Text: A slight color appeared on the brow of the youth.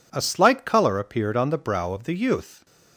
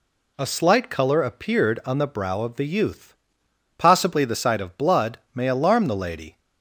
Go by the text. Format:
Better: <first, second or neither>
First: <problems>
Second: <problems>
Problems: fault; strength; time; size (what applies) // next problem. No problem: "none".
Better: first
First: none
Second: goes on to say "Possibly the sight of blood may alarm the lady"; strong; from 3.7 s on; 2.6 s long